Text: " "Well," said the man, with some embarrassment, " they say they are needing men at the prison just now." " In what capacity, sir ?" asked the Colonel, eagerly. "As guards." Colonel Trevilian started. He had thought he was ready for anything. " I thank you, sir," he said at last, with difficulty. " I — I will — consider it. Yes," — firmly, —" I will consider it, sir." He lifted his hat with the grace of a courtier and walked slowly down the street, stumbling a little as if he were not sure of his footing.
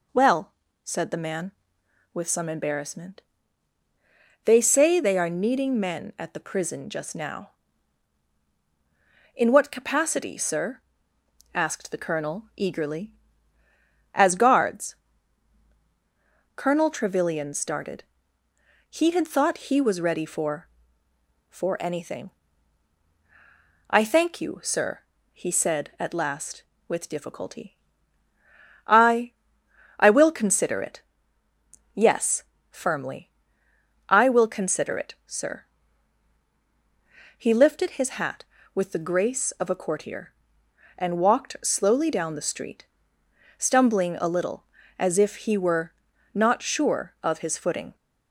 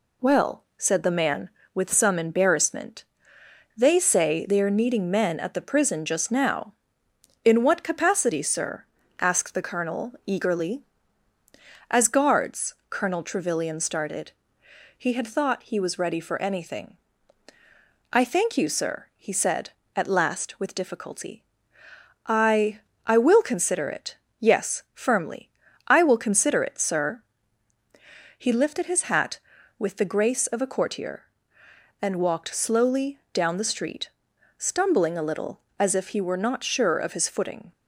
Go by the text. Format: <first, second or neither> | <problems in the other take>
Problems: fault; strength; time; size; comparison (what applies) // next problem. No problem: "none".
second | says "for" twice; at 21.4 s // pauses between "were" and "not"; at 45.9 s; 0.40 s long